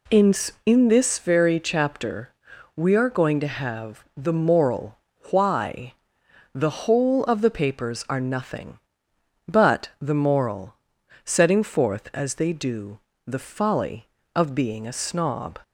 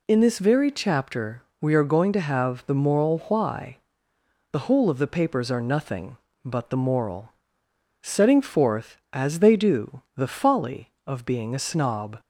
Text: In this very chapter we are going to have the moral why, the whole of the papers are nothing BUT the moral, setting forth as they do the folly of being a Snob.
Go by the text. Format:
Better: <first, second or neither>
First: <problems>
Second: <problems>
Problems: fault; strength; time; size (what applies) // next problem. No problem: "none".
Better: second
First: says "In" twice; at 0.6 s // pauses between "chapter" and "we"; at 2.3 s; 0.44 s long // pauses between "moral" and "why"; slight; at 4.9 s; 0.32 s long // pauses between "do" and "the"; slight; at 13.0 s; 0.26 s long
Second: pauses between "chapter" and "we"; slight; at 1.4 s; 0.18 s long